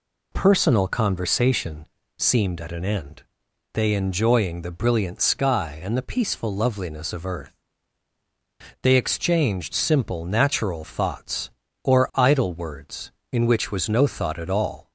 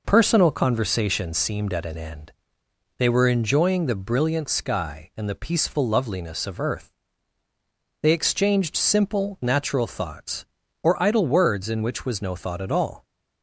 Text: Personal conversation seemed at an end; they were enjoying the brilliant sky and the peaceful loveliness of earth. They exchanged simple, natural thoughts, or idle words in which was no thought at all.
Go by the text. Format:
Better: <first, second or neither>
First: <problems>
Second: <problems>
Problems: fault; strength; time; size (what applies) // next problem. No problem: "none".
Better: second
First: pauses between "conversation" and "seemed"; slight; at 1.8 s; 0.32 s long // skips "were"; at 3.9 s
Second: none